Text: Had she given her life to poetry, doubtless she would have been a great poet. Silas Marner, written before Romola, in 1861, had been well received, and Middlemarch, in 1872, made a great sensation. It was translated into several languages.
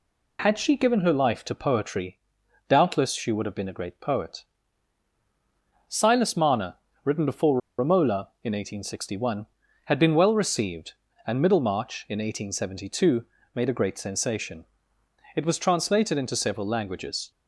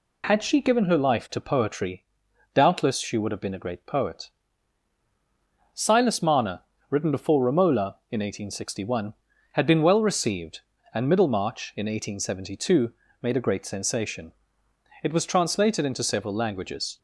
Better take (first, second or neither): second